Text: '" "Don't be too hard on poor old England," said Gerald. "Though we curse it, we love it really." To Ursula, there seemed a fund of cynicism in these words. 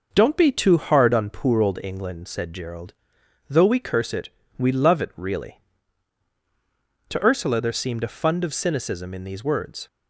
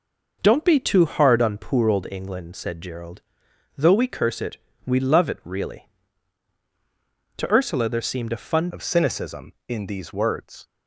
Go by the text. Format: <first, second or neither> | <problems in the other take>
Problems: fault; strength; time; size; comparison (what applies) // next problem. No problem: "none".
first | changes voice at "of"; from 8.7 s on; 1.9 s long